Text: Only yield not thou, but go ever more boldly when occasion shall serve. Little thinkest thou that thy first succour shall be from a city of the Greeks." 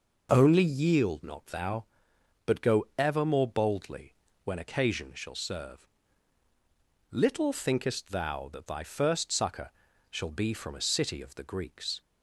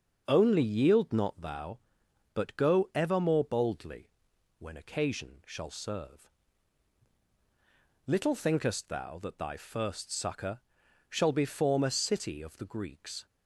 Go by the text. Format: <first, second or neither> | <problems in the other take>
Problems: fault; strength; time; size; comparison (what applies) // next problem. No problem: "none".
first | starts louder than the rest; until 1.2 s; 6.5 dB // pauses between "boldly" and "when"; noticeable; at 4.0 s; 0.48 s long; slight in the first // pauses between "succour" and "shall"; noticeable; at 10.6 s; 0.48 s long; also in the first // says "form" for "from"; at 11.4 s